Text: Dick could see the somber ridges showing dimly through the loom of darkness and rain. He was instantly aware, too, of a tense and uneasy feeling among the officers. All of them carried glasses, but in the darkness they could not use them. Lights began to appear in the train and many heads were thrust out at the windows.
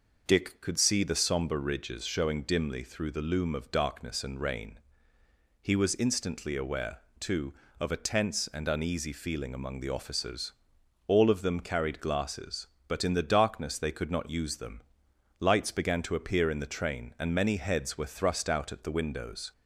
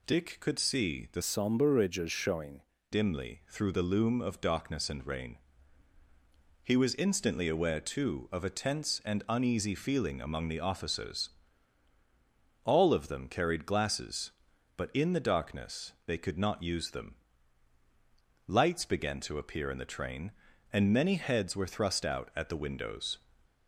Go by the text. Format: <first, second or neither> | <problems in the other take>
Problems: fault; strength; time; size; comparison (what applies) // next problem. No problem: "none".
first | changes voice from "somber" to "showing"; from 1.2 to 2.6 s; 1.4 s long